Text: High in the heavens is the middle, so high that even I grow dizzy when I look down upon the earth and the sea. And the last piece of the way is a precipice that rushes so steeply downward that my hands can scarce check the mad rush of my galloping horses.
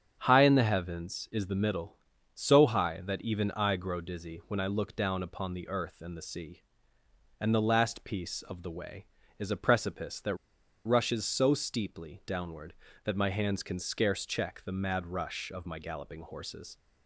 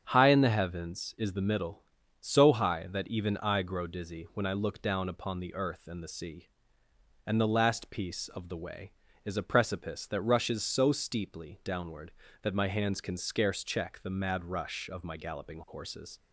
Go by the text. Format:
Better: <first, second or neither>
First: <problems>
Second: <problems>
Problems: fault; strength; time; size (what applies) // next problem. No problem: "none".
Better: second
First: starts louder than the rest; strong; until 1.2 s; 8 dB // pauses between "that" and "rushes"; noticeable; at 10.3 s; 0.50 s long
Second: starts louder than the rest; strong; until 1.0 s; 7.5 dB